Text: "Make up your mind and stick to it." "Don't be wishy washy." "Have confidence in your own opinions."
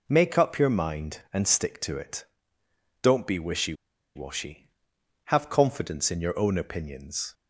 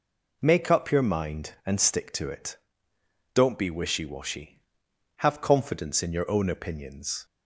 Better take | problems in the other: second | pauses between "wishy" and "washy"; at 3.7 s; 0.41 s long

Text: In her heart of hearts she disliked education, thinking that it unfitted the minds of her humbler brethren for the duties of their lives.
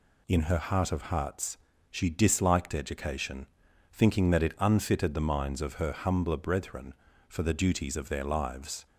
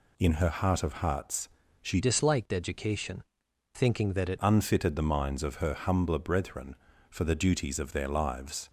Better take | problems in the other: first | pauses between "hearts" and "she"; slight; at 1.4 s; 0.32 s long; slight in the first // changes voice from "disliked" to "it"; from 2.0 to 4.3 s; 2.3 s long

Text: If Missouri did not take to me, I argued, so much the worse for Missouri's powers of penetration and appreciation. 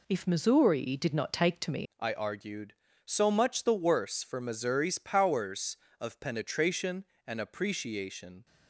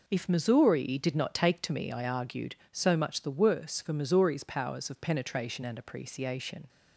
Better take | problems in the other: second | changes voice at "I"; from 1.9 s on; 6.5 s long

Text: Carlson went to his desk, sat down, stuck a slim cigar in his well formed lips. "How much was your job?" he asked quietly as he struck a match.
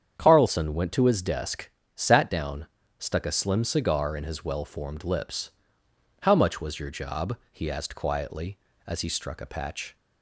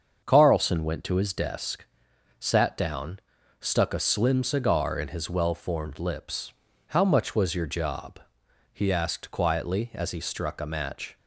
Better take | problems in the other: second | starts louder than the rest; strong; until 1.2 s; 8 dB; also in the second // says "patch" for "match"; at 9.4 s

